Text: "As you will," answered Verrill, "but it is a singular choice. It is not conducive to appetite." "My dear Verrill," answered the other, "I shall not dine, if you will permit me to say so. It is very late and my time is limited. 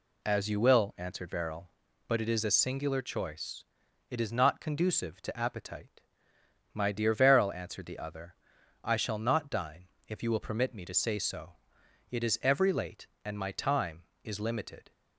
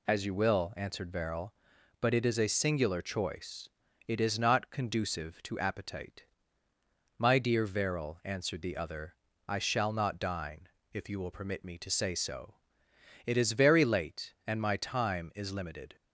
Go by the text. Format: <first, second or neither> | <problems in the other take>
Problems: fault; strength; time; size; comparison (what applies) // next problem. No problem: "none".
second | says "every" for "very"; at 12.4 s